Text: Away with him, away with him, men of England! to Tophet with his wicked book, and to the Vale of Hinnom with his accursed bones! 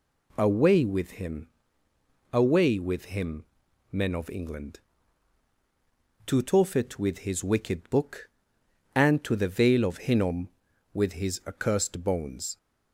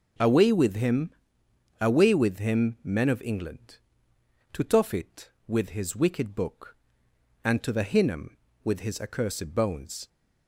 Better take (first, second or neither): first